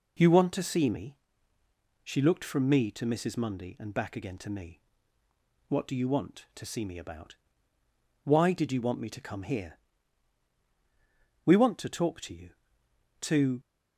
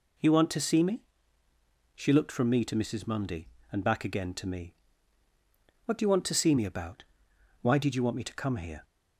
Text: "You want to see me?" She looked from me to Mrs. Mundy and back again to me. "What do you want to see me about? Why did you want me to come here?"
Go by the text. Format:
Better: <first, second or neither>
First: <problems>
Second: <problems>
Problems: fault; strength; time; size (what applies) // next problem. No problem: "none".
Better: second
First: goes on to say "We want to talk to you to"; strong; from 11.4 s on; 2.1 s long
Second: none